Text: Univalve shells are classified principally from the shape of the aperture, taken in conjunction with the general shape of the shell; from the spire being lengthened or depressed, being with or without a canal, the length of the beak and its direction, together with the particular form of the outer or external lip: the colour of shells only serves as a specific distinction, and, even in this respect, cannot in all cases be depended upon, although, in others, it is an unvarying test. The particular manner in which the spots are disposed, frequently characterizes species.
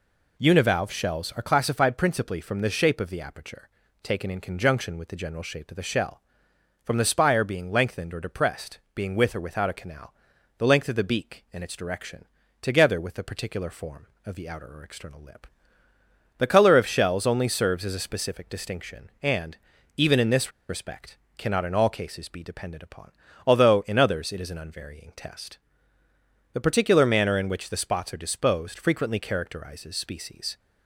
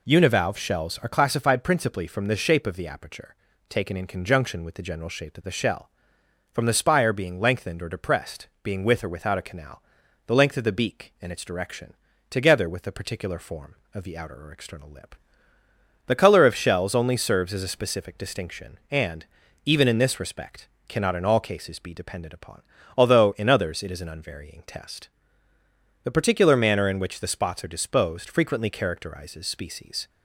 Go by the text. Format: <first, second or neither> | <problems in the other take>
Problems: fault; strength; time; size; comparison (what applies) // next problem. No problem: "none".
second | pauses between "this" and "respect"; slight; at 20.5 s; 0.18 s long